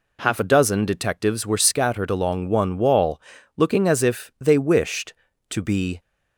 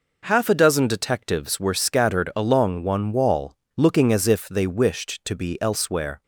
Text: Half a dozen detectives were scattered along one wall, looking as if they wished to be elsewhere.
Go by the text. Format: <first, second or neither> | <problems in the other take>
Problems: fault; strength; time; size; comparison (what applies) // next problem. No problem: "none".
second | stops before "elsewhere"; at 6.0 s